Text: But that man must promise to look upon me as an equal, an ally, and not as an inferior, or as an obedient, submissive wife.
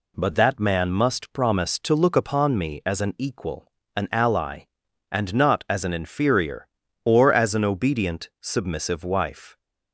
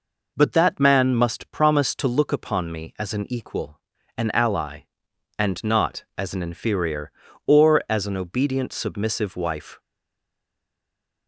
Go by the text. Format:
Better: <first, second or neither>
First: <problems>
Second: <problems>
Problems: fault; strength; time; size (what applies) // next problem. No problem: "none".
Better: first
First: none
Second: stays silent after the last word; noticeable; from 9.7 s on; 1.5 s long